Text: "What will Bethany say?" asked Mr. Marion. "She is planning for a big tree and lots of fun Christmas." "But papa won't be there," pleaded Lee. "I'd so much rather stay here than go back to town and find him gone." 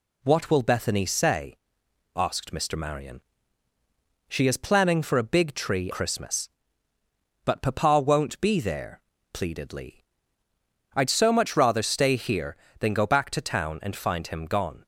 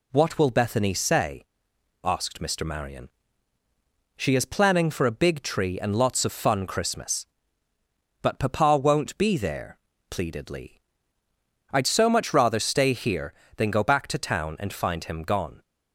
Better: second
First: skips "and lots of fun"; at 5.9 s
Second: none

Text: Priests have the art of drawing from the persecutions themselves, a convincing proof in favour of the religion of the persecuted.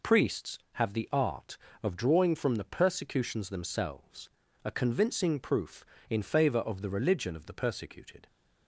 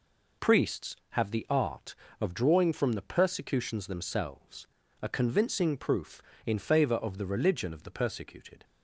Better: neither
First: none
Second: none

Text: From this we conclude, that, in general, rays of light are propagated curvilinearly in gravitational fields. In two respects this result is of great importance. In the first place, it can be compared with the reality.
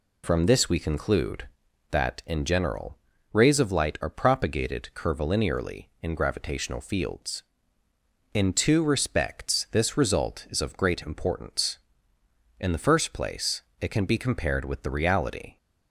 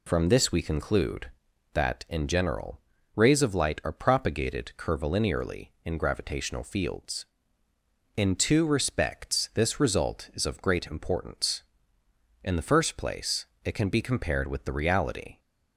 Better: neither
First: none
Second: none

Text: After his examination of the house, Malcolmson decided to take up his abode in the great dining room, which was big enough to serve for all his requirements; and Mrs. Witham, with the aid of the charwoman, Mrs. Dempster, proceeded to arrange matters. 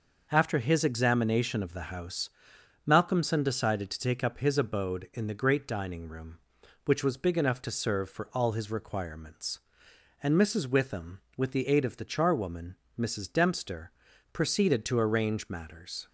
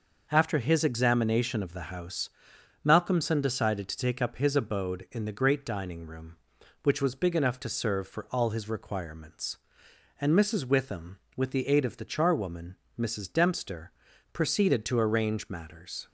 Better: neither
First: none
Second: none

